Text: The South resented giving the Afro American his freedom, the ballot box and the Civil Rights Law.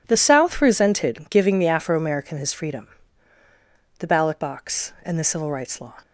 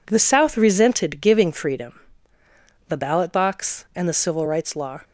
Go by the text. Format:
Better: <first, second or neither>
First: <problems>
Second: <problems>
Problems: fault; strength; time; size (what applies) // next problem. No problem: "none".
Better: first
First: none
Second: skips "the Afro American his"; at 1.5 s